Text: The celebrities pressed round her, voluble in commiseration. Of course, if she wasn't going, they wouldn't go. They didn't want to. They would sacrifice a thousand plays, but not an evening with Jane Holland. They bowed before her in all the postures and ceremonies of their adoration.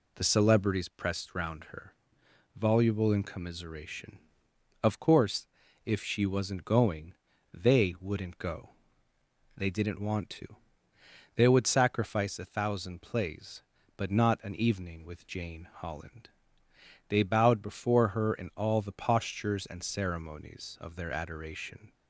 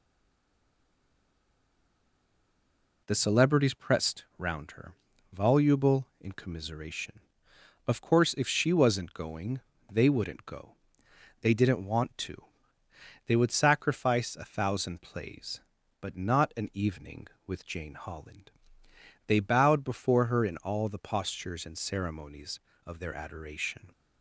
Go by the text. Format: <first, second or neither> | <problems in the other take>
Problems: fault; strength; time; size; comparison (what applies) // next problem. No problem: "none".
first | stays silent before the first word; strong; until 3.0 s; 3.0 s long